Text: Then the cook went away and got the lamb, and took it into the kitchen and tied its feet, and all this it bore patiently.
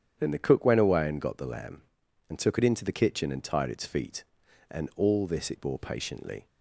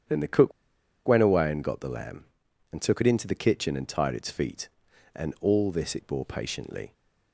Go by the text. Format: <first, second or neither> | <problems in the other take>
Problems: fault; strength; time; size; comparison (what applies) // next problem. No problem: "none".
first | starts louder than the rest; strong; until 1.6 s; 8.5 dB; strong in the first // pauses between "cook" and "went"; noticeable; at 0.5 s; 0.56 s long